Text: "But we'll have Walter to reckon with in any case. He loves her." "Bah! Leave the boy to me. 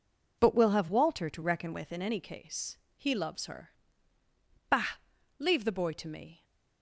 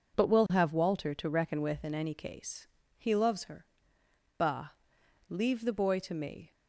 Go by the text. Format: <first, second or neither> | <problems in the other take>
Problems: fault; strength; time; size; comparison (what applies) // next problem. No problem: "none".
neither | none